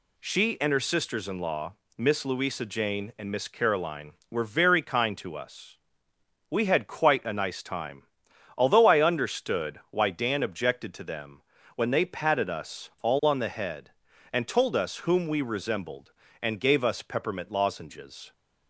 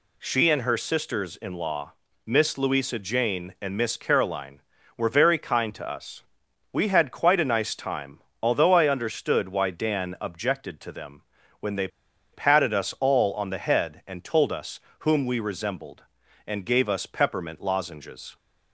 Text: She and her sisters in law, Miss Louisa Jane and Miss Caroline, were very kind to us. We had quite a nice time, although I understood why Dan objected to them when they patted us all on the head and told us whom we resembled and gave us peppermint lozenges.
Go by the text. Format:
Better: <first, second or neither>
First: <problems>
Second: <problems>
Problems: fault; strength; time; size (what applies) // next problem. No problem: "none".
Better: first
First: pauses between "them" and "when"; slight; at 11.4 s; 0.34 s long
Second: pauses between "them" and "when"; slight; at 11.2 s; 0.36 s long // pauses between "they" and "patted"; at 11.8 s; 0.45 s long // pauses between "us" and "whom"; slight; at 14.7 s; 0.20 s long